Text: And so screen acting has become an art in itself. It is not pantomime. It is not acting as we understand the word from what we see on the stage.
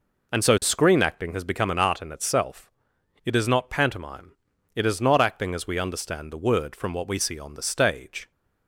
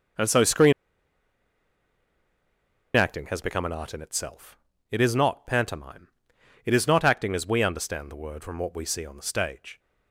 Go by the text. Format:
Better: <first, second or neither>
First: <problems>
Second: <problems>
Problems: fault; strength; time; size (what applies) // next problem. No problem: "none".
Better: first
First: none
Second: pauses between "screen" and "acting"; strong; at 0.7 s; 2.2 s long